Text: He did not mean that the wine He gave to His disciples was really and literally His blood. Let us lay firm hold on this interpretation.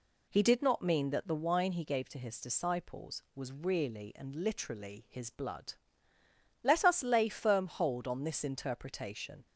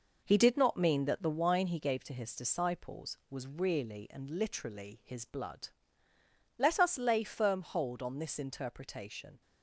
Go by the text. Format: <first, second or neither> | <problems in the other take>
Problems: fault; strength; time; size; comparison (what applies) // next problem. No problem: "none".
first | gets quieter; noticeable; throughout; 6 dB